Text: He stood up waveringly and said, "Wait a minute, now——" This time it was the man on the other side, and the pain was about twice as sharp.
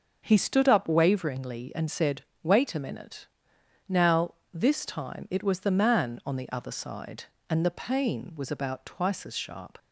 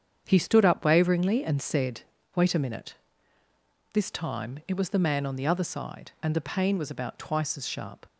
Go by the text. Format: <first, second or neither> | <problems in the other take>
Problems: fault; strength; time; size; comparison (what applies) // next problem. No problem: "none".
first | starts louder than the rest; strong; until 1.2 s; 8 dB; also in the first // skips "now"; at 3.4 s